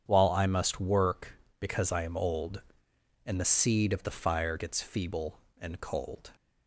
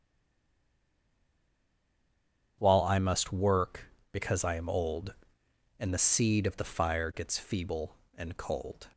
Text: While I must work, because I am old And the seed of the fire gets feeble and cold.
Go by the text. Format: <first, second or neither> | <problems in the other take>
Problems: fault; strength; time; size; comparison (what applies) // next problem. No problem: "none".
first | stays silent before the first word; strong; until 2.5 s; 2.5 s long // starts louder than the rest; strong; until 3.6 s; 8.5 dB; strong in the first